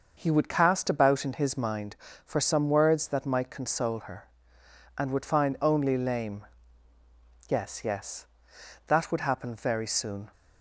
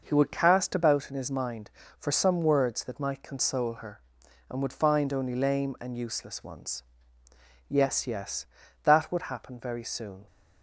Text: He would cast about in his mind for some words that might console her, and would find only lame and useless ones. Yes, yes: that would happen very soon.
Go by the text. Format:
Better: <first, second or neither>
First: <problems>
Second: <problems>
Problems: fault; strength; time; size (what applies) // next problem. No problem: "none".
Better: second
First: starts louder than the rest; noticeable; until 1.1 s; 6 dB // skips "and useless ones"; at 6.9 s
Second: none